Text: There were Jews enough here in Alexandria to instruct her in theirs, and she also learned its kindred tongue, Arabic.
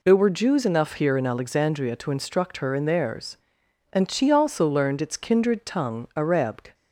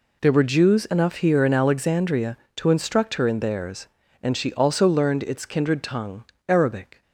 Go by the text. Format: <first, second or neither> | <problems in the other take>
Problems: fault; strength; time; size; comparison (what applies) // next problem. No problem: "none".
neither | none